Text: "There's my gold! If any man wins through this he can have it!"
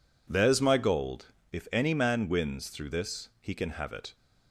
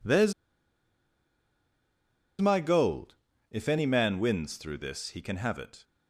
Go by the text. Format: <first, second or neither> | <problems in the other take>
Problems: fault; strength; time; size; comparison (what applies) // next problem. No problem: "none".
first | pauses between "There's" and "my"; strong; at 0.3 s; 2.0 s long